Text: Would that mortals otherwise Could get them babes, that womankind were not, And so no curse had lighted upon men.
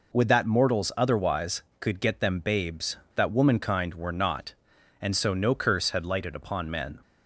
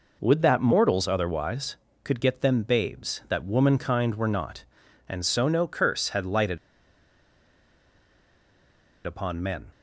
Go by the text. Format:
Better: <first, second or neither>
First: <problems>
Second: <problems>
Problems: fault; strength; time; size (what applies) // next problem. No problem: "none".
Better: first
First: none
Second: pauses between "lighted" and "upon"; strong; at 6.5 s; 2.4 s long